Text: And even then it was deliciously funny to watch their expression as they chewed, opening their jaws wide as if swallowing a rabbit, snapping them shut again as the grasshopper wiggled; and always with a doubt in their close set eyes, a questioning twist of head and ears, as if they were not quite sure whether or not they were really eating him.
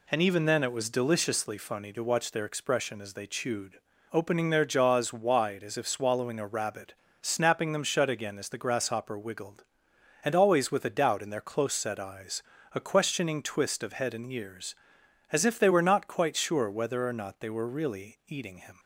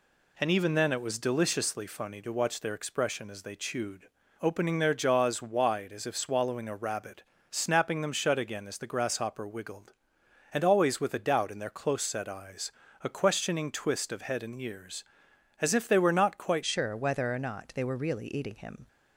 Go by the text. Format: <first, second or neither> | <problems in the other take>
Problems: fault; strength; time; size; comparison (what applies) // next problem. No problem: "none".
first | changes voice at "sure"; from 16.6 s on; 2.2 s long